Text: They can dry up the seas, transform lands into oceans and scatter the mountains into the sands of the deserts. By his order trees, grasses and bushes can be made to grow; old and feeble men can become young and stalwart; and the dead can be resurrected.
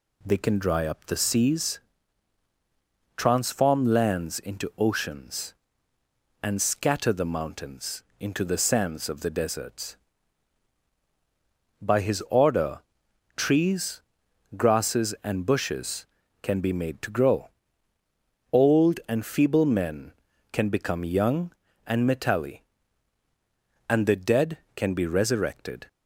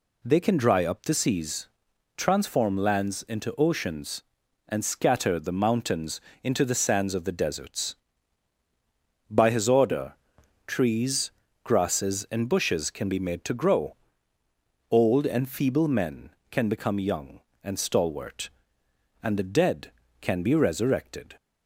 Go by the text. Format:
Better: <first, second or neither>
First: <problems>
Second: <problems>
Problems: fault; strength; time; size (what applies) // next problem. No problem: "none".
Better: second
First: pauses between "mountains" and "into"; slight; at 8.0 s; 0.18 s long // pauses between "order" and "trees"; noticeable; at 12.8 s; 0.54 s long // says "metalli" for "stalwart"; at 22.0 s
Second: pauses between "mountains" and "into"; slight; at 6.2 s; 0.22 s long // pauses between "order" and "trees"; noticeable; at 10.1 s; 0.50 s long